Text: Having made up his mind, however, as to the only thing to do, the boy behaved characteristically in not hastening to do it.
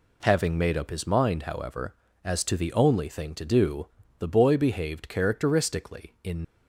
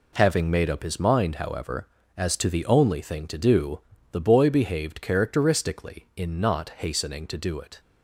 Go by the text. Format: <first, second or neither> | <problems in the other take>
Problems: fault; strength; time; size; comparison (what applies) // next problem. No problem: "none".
second | stops before "not hastening to do it"; at 6.4 s